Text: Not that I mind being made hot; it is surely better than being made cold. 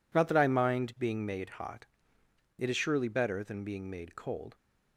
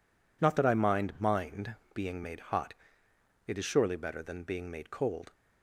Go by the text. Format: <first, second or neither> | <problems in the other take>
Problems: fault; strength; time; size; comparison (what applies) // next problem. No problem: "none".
first | says "mind" twice; at 1.1 s